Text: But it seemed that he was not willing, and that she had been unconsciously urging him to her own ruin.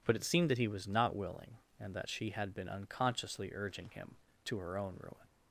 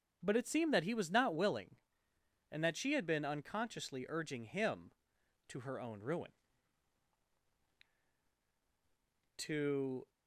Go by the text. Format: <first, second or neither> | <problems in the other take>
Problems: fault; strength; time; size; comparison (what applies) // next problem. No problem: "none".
first | starts louder than the rest; strong; until 1.2 s; 7 dB // goes on to say "To"; noticeable; from 9.3 s on; 0.70 s long